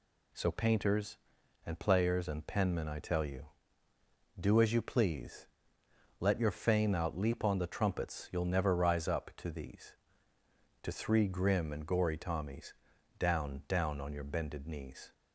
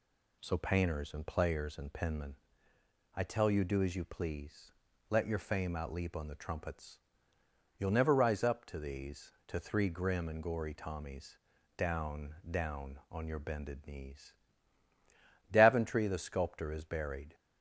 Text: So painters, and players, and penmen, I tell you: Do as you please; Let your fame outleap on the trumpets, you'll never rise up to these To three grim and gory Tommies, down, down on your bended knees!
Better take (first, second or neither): first